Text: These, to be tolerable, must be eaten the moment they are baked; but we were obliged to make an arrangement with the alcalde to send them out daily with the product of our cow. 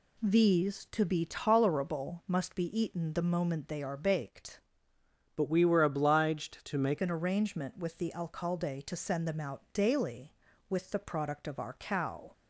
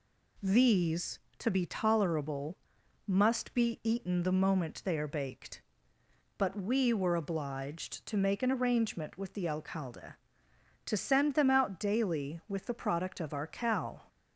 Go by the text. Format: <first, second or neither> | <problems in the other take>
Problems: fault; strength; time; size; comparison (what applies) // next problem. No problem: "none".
second | changes voice from "but" to "make"; from 5.3 to 6.9 s; 1.6 s long